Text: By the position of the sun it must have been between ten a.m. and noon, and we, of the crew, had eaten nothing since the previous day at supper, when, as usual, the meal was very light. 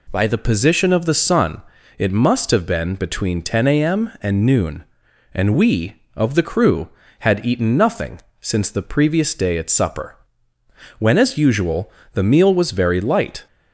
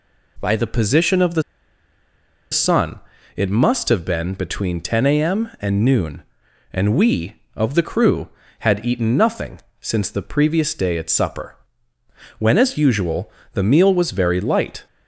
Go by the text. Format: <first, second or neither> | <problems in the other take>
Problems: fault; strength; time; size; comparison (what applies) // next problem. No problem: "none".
first | pauses between "the" and "sun"; at 1.4 s; 1.0 s long // pauses between "sun" and "it"; at 2.9 s; 0.38 s long; also in the first // pauses between "nothing" and "since"; slight; at 9.6 s; 0.18 s long; slight in the first